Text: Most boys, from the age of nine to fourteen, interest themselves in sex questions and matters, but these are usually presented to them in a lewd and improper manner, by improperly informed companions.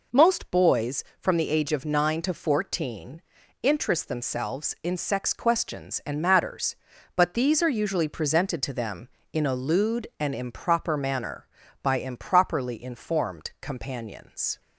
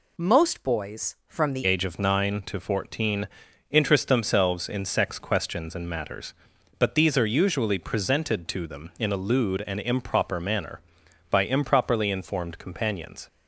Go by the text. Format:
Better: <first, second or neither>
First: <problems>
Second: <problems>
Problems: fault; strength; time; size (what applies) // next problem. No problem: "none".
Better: first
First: none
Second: changes voice at "age"; from 1.6 s on; 11.6 s long